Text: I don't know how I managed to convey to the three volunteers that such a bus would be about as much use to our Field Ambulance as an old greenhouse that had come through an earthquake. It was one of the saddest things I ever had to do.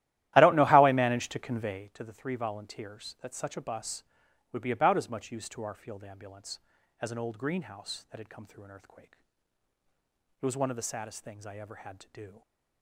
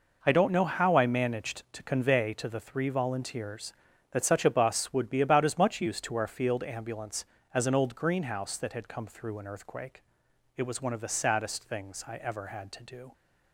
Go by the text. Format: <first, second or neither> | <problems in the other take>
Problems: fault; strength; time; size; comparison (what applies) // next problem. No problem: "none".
second | starts louder than the rest; strong; until 1.9 s; 14 dB